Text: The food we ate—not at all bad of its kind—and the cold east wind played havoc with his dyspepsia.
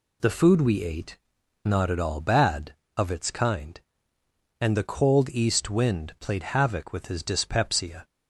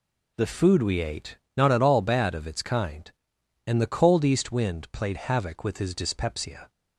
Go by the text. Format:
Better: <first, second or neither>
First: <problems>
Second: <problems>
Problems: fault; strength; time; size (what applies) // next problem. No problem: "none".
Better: neither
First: none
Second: none